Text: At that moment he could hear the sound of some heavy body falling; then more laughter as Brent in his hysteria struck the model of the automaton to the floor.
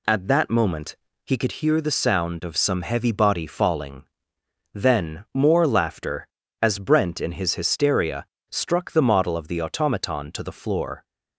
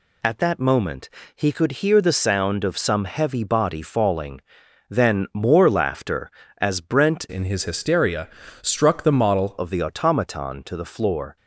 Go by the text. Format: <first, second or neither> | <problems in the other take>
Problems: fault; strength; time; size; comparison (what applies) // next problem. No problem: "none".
first | pauses between "moment" and "he"; slight; at 1.0 s; 0.26 s long; slight in the first // changes voice from "in" to "model"; from 7.2 to 9.5 s; 2.3 s long // pauses between "hysteria" and "struck"; slight; at 8.2 s; 0.34 s long; slight in the first